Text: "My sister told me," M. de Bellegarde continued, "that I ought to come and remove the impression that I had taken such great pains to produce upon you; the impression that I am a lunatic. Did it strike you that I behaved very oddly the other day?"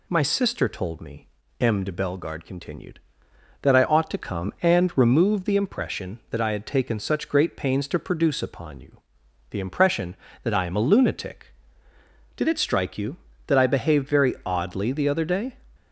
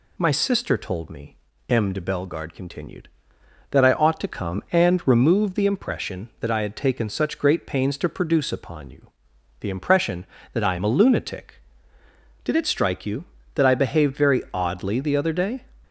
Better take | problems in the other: neither | none

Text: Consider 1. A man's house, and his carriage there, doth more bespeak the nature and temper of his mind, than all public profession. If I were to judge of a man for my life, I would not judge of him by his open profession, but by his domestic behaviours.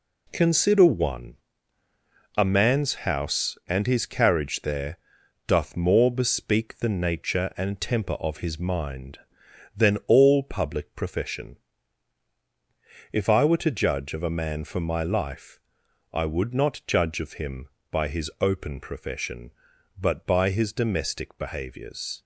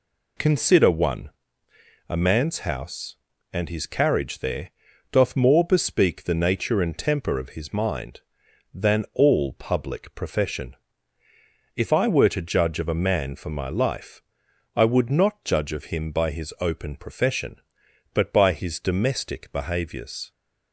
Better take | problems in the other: neither | none

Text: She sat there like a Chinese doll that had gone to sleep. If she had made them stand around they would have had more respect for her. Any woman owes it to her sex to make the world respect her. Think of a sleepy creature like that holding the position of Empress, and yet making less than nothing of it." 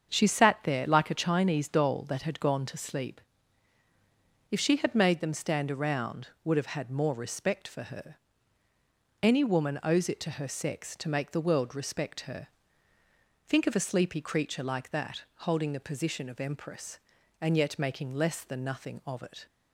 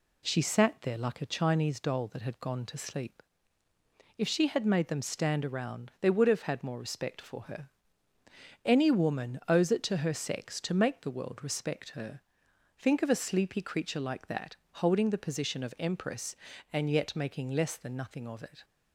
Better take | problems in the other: second | starts louder than the rest; strong; until 1.1 s; 7 dB // skips "they"; at 6.3 s // pauses between "that" and "holding"; slight; at 15.2 s; 0.16 s long; slight in the second

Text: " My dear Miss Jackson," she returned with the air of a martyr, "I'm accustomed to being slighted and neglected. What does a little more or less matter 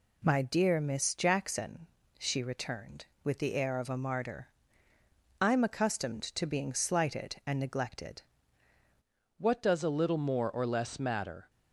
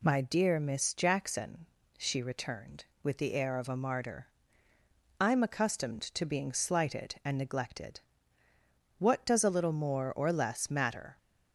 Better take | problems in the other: second | changes voice at "What"; from 9.3 s on; 2.1 s long

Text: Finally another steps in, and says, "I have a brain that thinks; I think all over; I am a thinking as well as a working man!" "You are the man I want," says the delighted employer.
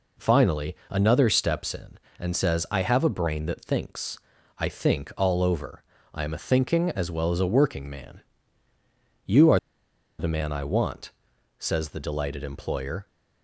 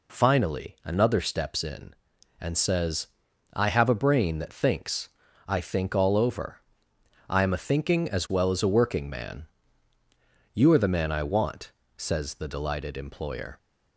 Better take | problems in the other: second | pauses between "Finally" and "another"; slight; at 0.7 s; 0.16 s long // pauses between "are" and "the"; noticeable; at 9.5 s; 0.60 s long

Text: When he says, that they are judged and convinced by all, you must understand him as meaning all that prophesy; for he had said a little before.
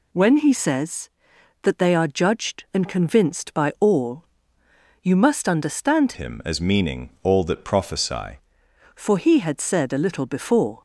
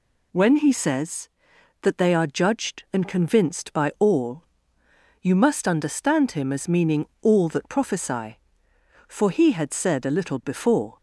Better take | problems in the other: second | changes voice from "him" to "prophesy"; from 6.1 to 8.3 s; 2.2 s long // pauses between "meaning" and "all"; slight; at 7.0 s; 0.16 s long

